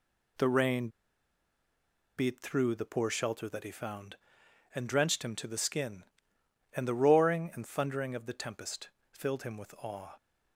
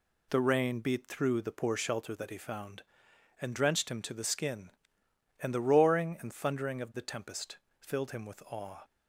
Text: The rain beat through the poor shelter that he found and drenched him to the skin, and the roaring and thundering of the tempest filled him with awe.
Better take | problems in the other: second | pauses between "rain" and "beat"; strong; at 0.8 s; 1.2 s long // pauses between "tempest" and "filled"; slight; at 8.8 s; 0.22 s long; slight in the second

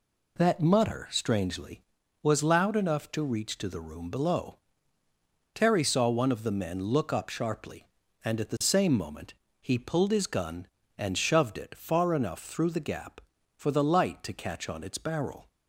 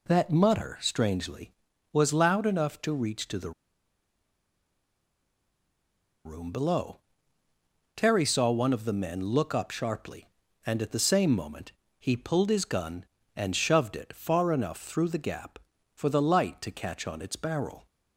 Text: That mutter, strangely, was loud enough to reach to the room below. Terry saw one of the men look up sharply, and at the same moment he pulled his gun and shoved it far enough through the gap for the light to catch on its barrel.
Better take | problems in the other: first | pauses between "the" and "room"; strong; at 3.5 s; 2.7 s long // pauses between "moment" and "he"; slight; at 11.7 s; 0.26 s long; slight in the first

